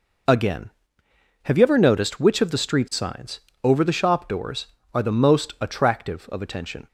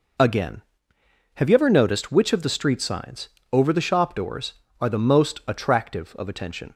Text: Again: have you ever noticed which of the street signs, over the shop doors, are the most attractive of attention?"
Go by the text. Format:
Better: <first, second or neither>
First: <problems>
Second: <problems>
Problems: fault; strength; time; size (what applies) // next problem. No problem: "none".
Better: neither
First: none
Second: none